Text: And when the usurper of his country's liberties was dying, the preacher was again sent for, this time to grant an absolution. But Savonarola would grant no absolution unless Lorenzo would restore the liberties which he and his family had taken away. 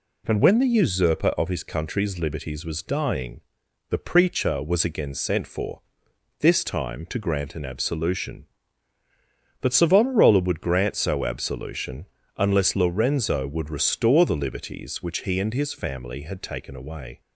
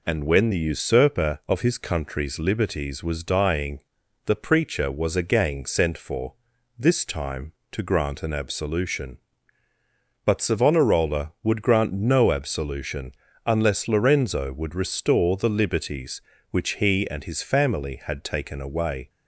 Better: second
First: says "so" for "no"; at 10.9 s // pauses between "absolution" and "unless"; slight; at 12.0 s; 0.30 s long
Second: pauses between "absolution" and "unless"; slight; at 13.1 s; 0.34 s long

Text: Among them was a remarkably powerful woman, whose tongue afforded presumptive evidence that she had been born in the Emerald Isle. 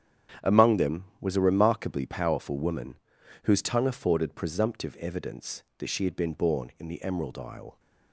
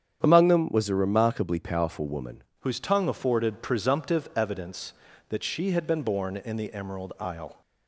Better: first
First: starts louder than the rest; strong; until 1.5 s; 9 dB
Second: starts louder than the rest; strong; until 1.2 s; 8.5 dB // changes voice at "whose"; from 2.6 s on; 5.0 s long

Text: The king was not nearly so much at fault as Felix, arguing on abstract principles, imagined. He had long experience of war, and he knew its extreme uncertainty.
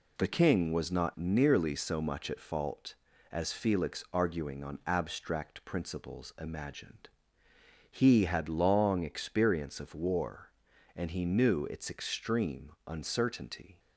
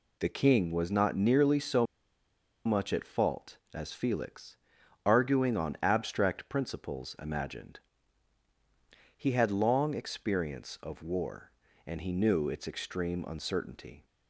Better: first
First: none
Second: pauses between "so" and "much"; noticeable; at 1.8 s; 0.79 s long

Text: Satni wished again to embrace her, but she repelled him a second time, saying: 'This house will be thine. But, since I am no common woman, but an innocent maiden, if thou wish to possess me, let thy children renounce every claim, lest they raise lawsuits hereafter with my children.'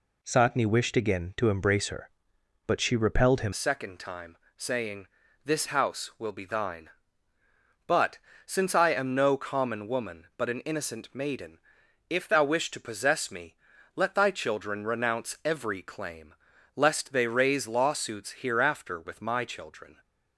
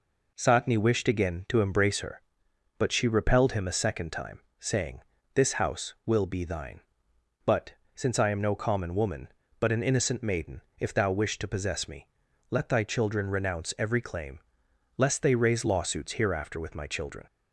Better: second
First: changes voice at "a"; from 3.5 s on; 16.4 s long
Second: none

